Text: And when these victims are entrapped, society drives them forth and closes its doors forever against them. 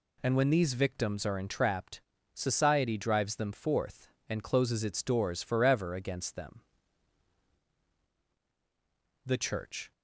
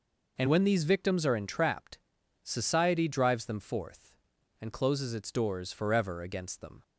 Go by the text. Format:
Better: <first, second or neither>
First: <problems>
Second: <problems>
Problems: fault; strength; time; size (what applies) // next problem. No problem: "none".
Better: second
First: goes on to say "The Church"; noticeable; from 9.2 s on; 0.66 s long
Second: none